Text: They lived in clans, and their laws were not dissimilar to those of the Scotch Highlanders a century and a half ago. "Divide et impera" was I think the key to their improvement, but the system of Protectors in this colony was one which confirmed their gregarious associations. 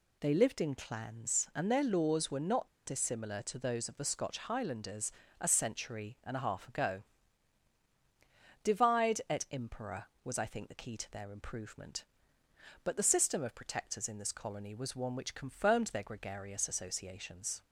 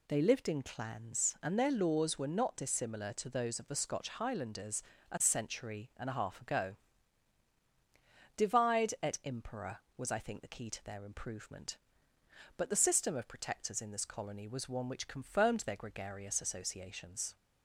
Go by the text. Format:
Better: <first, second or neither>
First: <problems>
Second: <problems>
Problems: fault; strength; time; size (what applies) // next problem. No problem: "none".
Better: second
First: pauses between "not" and "dissimilar"; slight; at 2.6 s; 0.17 s long // pauses between "Highlanders" and "a"; slight; at 5.1 s; 0.26 s long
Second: pauses between "Highlanders" and "a"; slight; at 4.8 s; 0.26 s long